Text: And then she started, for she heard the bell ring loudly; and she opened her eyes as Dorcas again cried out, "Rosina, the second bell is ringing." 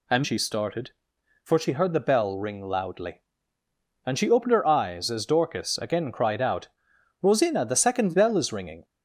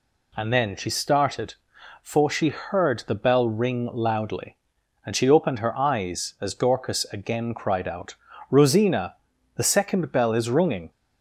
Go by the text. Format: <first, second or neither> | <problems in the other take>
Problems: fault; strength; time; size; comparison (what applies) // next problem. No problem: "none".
second | skips "then"; at 0.2 s